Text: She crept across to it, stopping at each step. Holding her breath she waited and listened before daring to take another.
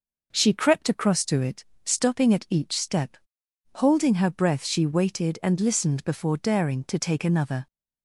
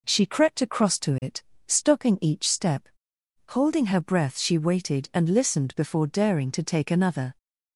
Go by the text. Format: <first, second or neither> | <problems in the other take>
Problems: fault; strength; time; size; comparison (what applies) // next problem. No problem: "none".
first | skips "at"; at 2.1 s